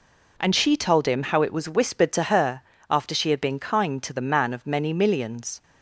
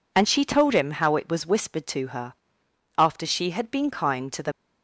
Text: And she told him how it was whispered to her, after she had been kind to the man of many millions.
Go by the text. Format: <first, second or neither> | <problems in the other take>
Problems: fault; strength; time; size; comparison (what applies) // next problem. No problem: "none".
first | stops before "man of many millions"; at 4.5 s